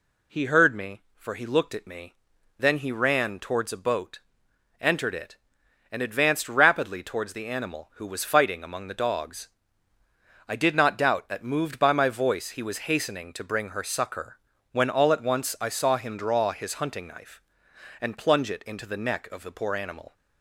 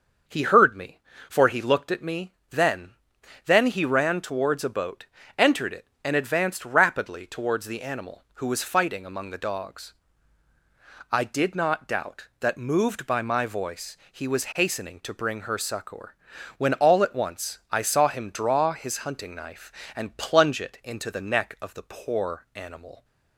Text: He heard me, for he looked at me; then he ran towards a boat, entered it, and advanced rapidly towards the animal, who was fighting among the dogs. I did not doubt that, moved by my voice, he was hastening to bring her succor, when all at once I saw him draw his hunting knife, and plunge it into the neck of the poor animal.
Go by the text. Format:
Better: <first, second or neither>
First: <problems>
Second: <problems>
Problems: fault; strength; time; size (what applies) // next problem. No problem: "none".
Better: first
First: none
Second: starts louder than the rest; until 1.5 s; 6.5 dB // says "then" twice; at 3.4 s